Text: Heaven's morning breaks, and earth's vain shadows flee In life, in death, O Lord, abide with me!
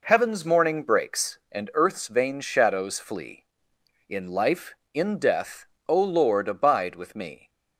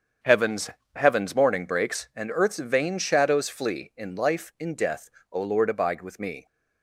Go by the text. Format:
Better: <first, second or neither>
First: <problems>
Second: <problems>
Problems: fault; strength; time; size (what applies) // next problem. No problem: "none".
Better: first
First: none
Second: starts louder than the rest; strong; until 1.4 s; 7.5 dB // says "Heaven's" twice; at 0.9 s